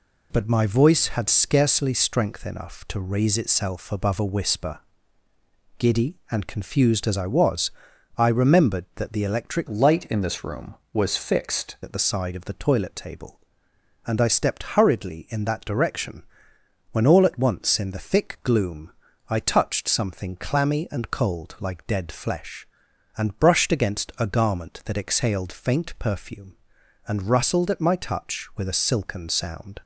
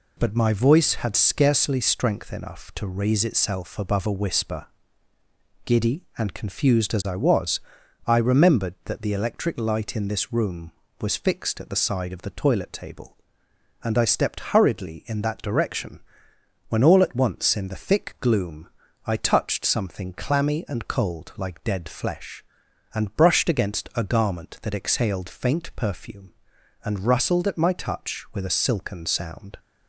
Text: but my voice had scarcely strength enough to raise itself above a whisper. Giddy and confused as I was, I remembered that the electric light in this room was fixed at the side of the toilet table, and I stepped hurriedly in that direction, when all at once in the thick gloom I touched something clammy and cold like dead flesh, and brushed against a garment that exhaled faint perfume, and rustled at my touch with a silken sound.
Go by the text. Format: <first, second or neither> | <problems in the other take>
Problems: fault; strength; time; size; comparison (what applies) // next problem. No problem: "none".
second | changes voice from "light" to "fixed"; from 9.6 to 11.7 s; 2.1 s long // pauses between "gloom" and "I"; at 18.9 s; 0.38 s long; also in the second